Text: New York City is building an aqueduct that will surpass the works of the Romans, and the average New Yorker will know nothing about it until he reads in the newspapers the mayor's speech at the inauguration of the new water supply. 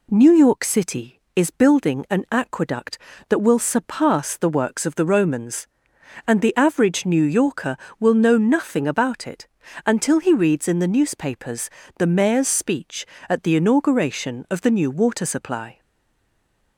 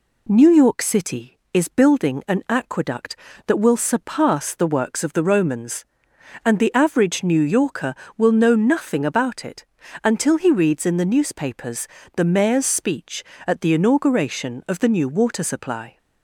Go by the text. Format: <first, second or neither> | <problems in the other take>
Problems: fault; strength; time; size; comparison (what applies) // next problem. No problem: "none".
second | pauses between "it" and "until"; at 9.4 s; 0.40 s long; also in the second // pauses between "newspapers" and "the"; slight; at 11.6 s; 0.30 s long; slight in the second // stays silent after the last word; from 15.7 s on; 1.0 s long